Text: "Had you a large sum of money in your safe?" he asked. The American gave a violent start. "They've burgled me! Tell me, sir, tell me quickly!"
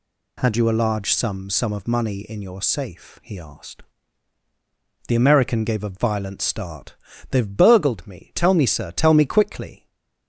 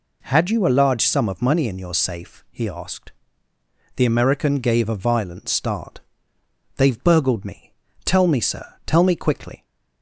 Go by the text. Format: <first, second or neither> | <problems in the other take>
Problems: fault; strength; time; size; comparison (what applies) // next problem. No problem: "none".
second | says "sum" twice; at 1.4 s // stays silent after the last word; slight; from 9.7 s on; 0.5 s long